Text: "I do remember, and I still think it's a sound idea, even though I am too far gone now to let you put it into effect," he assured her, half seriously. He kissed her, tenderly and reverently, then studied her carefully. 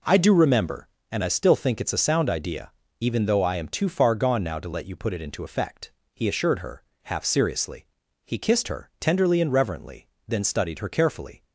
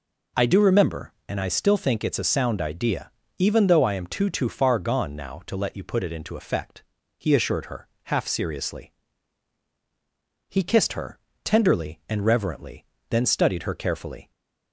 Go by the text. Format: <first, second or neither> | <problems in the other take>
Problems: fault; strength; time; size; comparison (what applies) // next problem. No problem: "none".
first | says "too" twice; at 4.2 s